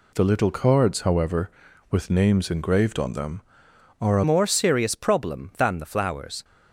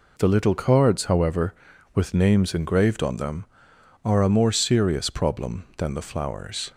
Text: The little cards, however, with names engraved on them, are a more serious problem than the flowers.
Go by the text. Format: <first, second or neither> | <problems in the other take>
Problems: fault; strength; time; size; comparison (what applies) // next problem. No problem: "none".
second | changes voice at "more"; from 4.2 s on; 2.2 s long